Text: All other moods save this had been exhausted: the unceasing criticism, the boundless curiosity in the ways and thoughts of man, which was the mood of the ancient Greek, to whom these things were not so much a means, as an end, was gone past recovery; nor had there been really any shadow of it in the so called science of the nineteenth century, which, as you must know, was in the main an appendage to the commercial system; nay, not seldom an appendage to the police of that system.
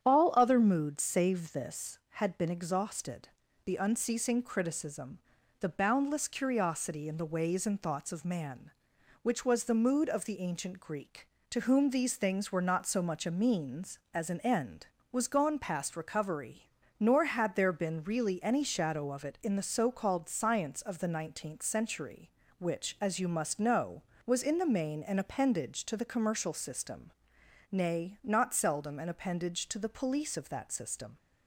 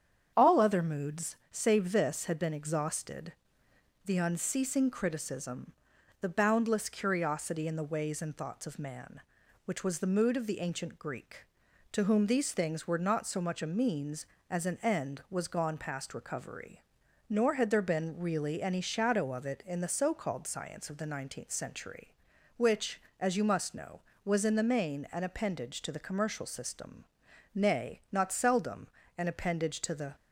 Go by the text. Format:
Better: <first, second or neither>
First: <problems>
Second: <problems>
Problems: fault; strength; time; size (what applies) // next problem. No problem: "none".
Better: first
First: starts louder than the rest; strong; until 1.0 s; 9 dB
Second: starts louder than the rest; strong; until 1.3 s; 8.5 dB // pauses between "moods" and "save"; slight; at 1.3 s; 0.16 s long // pauses between "seldom" and "an"; slight; at 28.8 s; 0.30 s long // stops before "police of that system"; at 30.1 s